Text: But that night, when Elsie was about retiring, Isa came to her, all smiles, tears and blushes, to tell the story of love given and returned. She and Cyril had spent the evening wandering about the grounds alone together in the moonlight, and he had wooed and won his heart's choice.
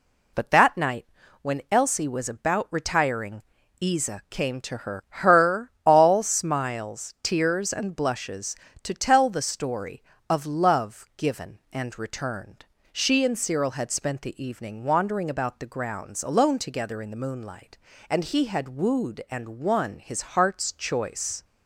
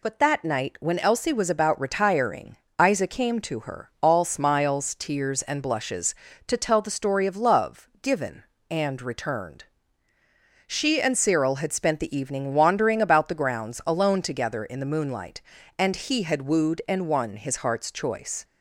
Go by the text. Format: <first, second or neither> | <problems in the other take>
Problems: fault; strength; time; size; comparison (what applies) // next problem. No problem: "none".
second | says "her" twice; at 5.0 s